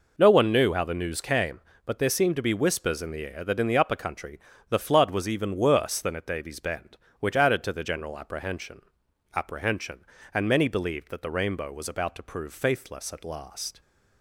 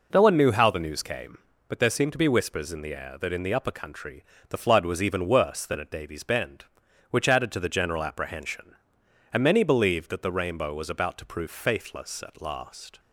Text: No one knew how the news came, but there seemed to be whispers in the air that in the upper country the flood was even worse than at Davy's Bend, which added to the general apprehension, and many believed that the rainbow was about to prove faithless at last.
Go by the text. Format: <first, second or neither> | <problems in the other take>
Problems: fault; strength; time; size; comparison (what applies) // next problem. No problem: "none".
second | pauses between "country" and "the"; slight; at 4.3 s; 0.30 s long; slight in the second // says "apprehension" twice; at 9.3 s